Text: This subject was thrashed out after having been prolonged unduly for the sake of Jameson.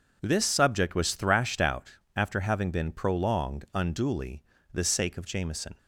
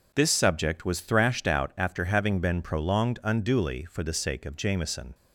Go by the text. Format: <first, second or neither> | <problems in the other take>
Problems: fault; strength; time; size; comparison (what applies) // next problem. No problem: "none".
second | pauses between "out" and "after"; slight; at 1.9 s; 0.18 s long // skips "for"; at 4.5 s